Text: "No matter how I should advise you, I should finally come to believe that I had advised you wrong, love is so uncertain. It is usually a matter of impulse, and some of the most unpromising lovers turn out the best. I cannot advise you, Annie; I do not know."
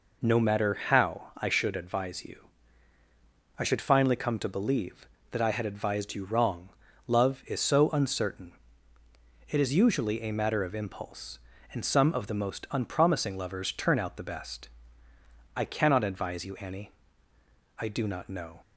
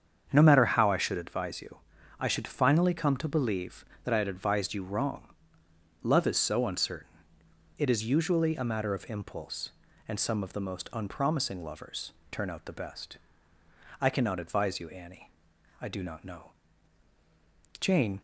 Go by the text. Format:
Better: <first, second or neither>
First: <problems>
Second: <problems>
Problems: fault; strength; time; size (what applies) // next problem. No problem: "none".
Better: first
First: none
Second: starts louder than the rest; strong; until 1.3 s; 7.5 dB // pauses between "lovers" and "turn"; slight; at 12.1 s; 0.18 s long // goes on to say "Jane"; slight; from 17.8 s on; 0.40 s long